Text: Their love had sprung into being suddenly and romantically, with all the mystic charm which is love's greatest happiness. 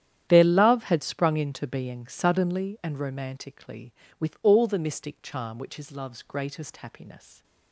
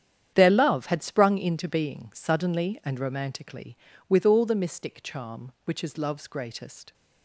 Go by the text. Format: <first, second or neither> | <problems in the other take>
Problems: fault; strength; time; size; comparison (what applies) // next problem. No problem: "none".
first | starts louder than the rest; strong; until 1.3 s; 9 dB; strong in the first // stops before "happiness"; at 6.9 s